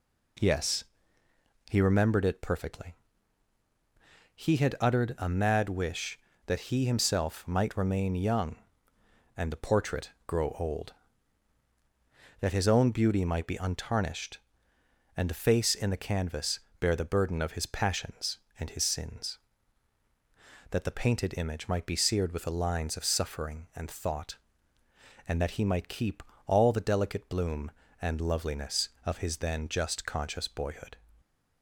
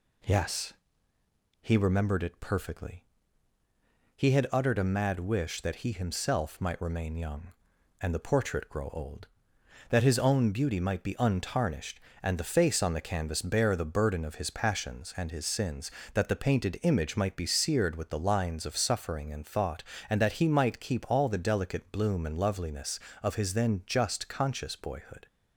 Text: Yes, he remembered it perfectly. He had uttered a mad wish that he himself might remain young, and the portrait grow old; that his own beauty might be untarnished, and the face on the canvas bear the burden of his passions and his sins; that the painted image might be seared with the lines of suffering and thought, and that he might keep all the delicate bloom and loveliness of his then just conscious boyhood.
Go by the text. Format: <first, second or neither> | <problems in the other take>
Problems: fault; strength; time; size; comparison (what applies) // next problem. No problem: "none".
second | pauses between "portrait" and "grow"; slight; at 10.0 s; 0.18 s long // says "in" for "on"; at 15.7 s // pauses between "canvas" and "bear"; slight; at 16.5 s; 0.20 s long // pauses between "keep" and "all"; slight; at 26.2 s; 0.24 s long